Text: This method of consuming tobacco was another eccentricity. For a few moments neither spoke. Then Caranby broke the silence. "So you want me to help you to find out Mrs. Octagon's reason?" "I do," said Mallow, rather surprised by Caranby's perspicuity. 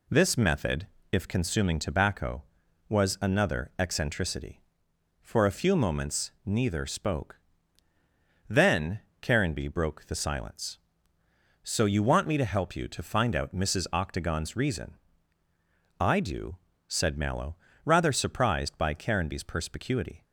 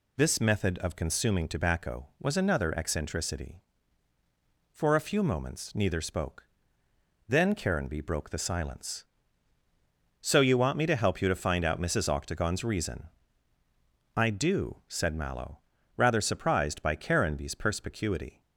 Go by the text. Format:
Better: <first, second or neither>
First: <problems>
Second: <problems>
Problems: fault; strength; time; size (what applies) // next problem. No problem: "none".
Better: second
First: says "if" for "of"; at 1.1 s // pauses between "moments" and "neither"; slight; at 6.3 s; 0.16 s long // pauses between "Then" and "Caranby"; slight; at 9.0 s; 0.20 s long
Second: none